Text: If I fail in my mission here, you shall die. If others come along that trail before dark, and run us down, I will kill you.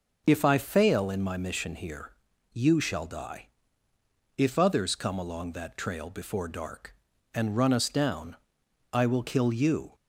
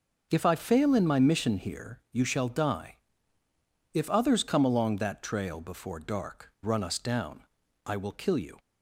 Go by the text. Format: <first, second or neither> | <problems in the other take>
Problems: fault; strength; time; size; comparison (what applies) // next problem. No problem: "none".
first | starts louder than the rest; until 1.3 s; 6.5 dB // skips "and"; at 6.5 s